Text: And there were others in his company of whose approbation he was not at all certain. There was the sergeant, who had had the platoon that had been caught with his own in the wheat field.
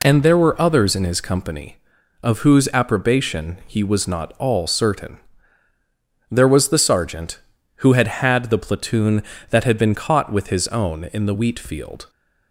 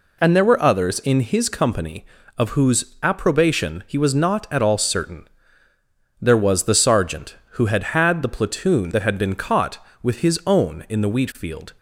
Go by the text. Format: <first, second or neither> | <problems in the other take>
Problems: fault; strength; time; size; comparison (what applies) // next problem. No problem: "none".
second | skips "at"; at 4.3 s